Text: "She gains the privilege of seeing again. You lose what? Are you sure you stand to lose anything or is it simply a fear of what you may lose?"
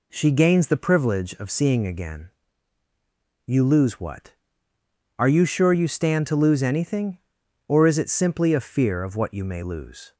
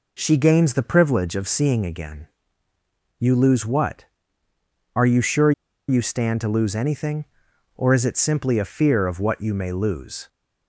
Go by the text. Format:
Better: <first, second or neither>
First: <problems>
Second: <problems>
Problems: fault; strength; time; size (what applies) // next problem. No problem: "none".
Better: first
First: none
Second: pauses between "sure" and "you"; at 5.5 s; 0.36 s long